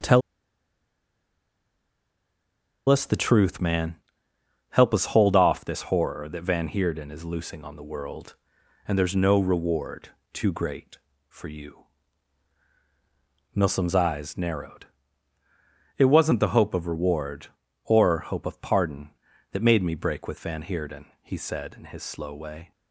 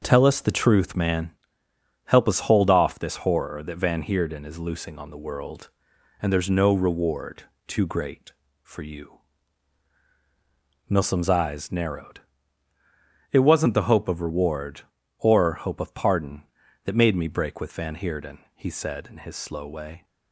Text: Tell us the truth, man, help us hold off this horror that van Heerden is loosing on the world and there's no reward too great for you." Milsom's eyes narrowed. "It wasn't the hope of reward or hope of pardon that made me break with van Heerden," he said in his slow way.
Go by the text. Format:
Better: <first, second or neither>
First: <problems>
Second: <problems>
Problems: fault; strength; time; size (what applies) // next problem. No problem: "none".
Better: second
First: pauses between "Tell" and "us"; strong; at 0.2 s; 2.6 s long // pauses between "reward" and "too"; slight; at 10.0 s; 0.24 s long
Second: pauses between "reward" and "too"; slight; at 7.4 s; 0.24 s long